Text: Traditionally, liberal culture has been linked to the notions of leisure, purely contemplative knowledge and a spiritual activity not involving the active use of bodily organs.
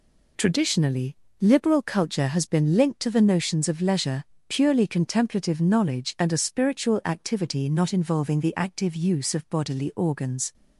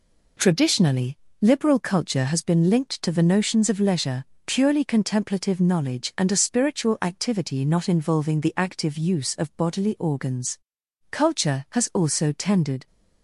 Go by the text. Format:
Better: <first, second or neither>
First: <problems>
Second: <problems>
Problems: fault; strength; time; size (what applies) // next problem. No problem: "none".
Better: first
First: none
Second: goes on to say "Culture has also tended"; strong; from 11.1 s on; 1.7 s long